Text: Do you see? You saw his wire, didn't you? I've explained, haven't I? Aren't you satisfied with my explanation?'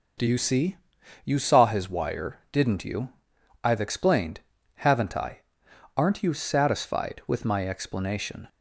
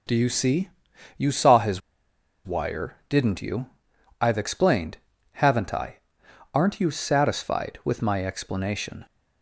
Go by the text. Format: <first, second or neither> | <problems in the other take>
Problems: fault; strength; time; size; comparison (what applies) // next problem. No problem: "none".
first | pauses between "his" and "wire"; noticeable; at 1.8 s; 0.65 s long